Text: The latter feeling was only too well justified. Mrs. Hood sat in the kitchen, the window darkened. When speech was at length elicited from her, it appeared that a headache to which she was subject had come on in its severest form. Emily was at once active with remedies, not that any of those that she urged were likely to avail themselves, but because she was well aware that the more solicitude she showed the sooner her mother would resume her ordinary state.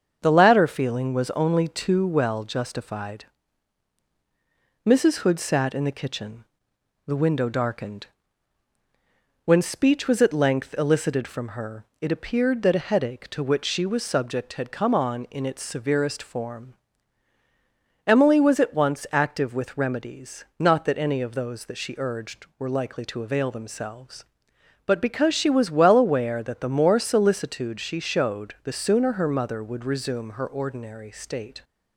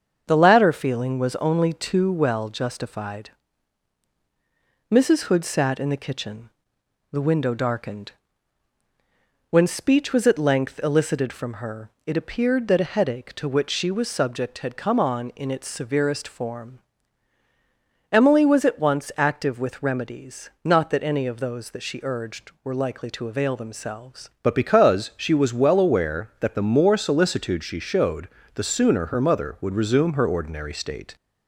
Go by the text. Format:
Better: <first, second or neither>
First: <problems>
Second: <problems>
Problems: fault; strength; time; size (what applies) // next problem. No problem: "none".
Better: first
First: starts louder than the rest; until 1.2 s; 7 dB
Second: starts louder than the rest; until 1.2 s; 7 dB // changes voice at "but"; from 24.4 s on; 6.7 s long // pauses between "showed" and "the"; slight; at 28.2 s; 0.24 s long